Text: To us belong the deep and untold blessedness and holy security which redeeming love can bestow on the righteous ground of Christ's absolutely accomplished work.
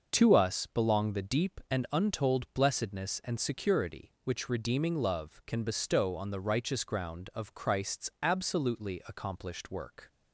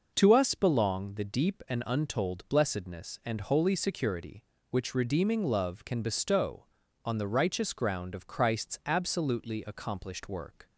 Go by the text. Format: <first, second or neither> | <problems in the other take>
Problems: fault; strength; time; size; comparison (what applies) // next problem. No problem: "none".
second | starts louder than the rest; noticeable; until 1.1 s; 6 dB // skips "holy"; at 3.3 s